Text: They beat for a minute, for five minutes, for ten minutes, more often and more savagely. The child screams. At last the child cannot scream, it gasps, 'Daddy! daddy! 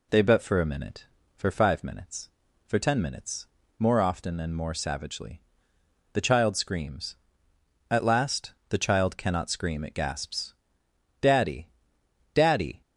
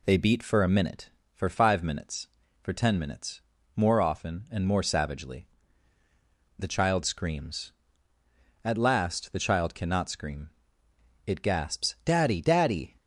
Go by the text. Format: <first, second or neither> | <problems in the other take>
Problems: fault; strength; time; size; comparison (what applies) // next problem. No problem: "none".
second | says "bet" for "beat"; at 0.2 s // pauses between "last" and "the"; slight; at 8.5 s; 0.18 s long